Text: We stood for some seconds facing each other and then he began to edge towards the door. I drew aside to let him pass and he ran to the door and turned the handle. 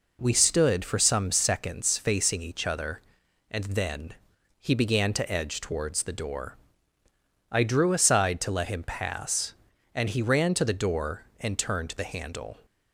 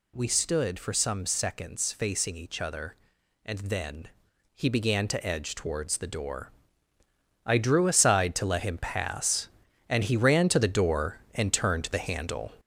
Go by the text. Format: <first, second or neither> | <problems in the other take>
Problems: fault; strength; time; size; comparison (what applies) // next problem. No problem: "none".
first | gets louder; noticeable; throughout; 5.5 dB // pauses between "then" and "he"; noticeable; at 4.0 s; 0.48 s long; noticeable in the first